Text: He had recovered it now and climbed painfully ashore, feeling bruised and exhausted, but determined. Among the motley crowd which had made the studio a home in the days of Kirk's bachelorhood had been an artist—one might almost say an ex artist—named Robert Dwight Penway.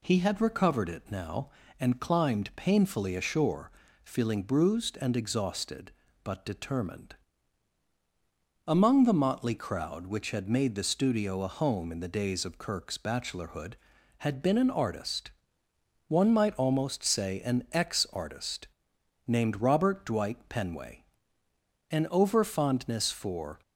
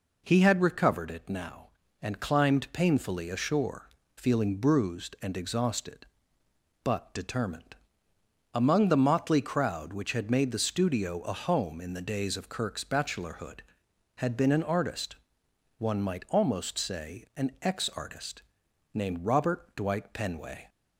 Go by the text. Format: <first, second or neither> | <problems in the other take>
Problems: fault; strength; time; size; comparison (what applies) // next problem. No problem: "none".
second | goes on to say "An over fondness for"; strong; from 21.9 s on; 1.7 s long